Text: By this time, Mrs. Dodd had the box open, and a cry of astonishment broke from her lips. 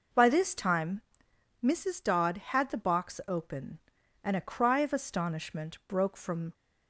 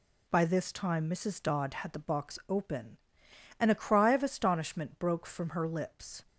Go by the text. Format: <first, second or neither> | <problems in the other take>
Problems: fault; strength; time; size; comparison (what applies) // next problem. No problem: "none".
second | stops before "her lips"; at 6.5 s